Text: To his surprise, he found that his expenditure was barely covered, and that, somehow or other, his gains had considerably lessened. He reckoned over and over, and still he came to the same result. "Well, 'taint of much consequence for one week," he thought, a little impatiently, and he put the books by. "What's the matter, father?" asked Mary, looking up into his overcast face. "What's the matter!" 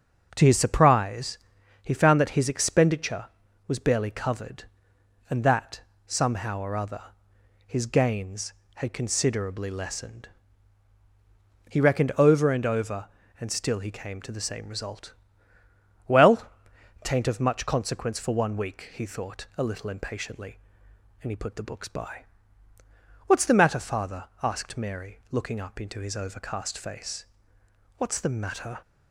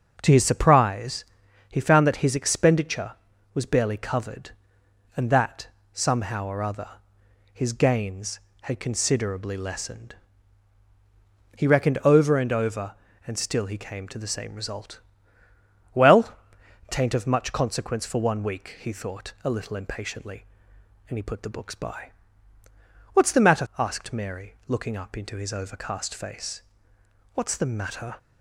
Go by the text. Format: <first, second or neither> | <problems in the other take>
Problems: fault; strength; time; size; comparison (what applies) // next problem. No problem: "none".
first | skips "father"; at 23.7 s